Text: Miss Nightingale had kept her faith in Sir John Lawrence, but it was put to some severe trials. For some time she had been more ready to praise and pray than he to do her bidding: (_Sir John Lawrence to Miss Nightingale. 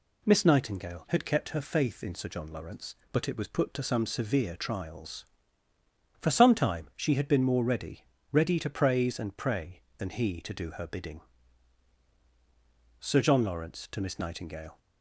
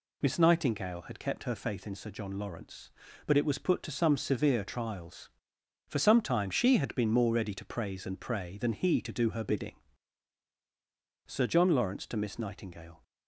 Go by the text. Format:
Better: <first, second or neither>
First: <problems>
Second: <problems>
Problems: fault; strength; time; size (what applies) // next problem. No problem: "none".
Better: second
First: says "ready" twice; at 8.3 s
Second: none